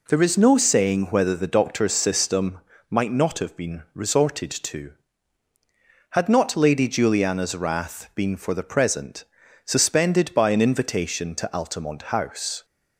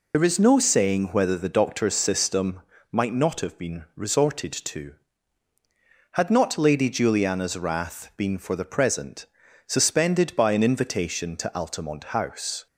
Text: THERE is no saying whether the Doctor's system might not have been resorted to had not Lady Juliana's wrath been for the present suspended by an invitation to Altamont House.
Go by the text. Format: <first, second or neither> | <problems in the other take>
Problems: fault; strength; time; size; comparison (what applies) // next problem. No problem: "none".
first | loses the start of "THERE"; at 0.1 s; 55 ms // pauses between "system" and "might"; slight; at 2.6 s; 0.32 s long; slight in the first // pauses between "present" and "suspended"; at 9.2 s; 0.40 s long; also in the first